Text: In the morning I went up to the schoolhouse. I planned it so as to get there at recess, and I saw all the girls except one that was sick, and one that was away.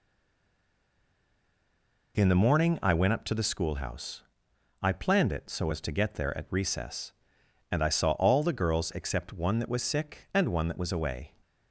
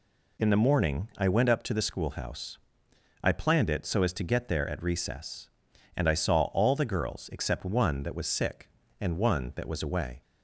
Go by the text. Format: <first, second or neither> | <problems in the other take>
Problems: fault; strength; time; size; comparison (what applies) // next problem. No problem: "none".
second | stays silent before the first word; until 2.1 s; 2.1 s long